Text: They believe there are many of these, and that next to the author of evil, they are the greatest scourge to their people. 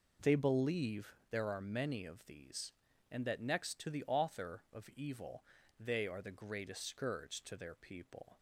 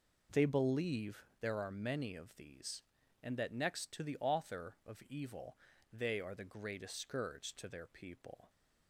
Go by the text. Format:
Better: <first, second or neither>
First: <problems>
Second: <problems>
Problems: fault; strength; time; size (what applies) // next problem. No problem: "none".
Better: neither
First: none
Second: none